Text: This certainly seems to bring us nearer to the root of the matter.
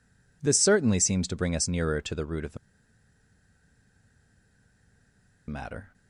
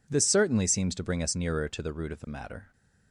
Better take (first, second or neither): second